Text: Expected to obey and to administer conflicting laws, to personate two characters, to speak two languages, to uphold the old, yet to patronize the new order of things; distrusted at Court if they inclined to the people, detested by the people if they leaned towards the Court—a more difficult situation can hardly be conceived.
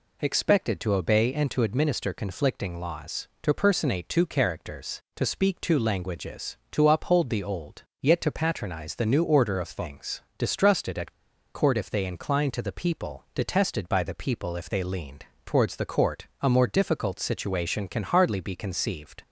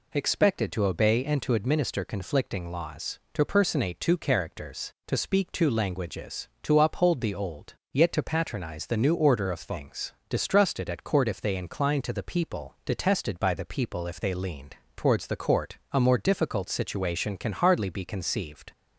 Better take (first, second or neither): second